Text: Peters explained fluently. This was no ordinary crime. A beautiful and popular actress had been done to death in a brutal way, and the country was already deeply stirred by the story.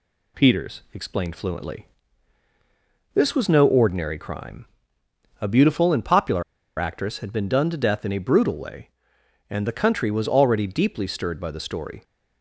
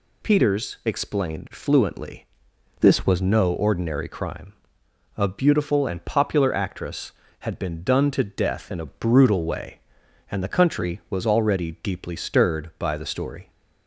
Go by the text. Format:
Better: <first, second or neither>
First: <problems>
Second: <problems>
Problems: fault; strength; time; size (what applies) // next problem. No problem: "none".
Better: second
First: pauses between "popular" and "actress"; at 6.4 s; 0.36 s long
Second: none